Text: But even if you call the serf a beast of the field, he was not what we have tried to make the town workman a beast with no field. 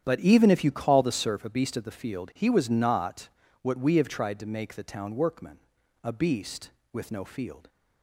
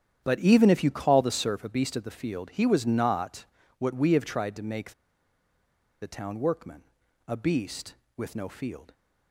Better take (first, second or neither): first